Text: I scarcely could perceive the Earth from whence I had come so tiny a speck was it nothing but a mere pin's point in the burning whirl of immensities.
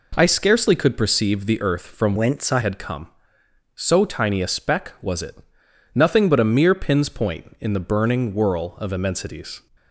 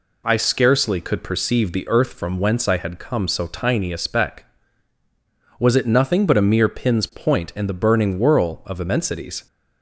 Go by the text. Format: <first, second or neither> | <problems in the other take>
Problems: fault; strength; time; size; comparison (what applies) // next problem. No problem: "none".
second | changes voice from "whence" to "I"; from 2.1 to 2.6 s; 0.5 s long // pauses between "it" and "nothing"; noticeable; at 5.3 s; 0.60 s long